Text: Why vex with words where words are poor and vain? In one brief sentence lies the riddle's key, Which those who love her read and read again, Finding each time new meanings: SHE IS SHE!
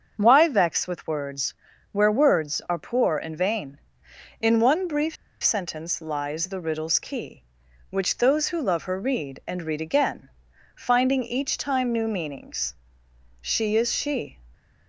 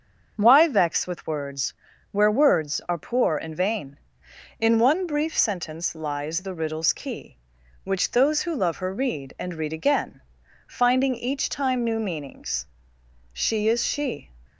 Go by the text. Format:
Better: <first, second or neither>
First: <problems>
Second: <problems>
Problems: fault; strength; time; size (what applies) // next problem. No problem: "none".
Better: second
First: starts louder than the rest; until 1.1 s; 6.5 dB // pauses between "words" and "where"; at 1.5 s; 0.38 s long // pauses between "brief" and "sentence"; slight; at 5.1 s; 0.28 s long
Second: starts louder than the rest; until 1.3 s; 6.5 dB // pauses between "words" and "where"; at 1.7 s; 0.38 s long